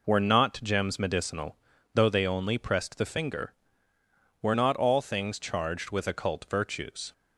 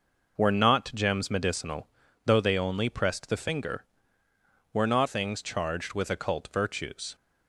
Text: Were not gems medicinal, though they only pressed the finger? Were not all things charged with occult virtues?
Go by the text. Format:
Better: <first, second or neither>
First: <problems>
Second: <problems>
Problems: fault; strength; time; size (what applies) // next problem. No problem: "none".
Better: first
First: none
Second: skips "all"; at 5.0 s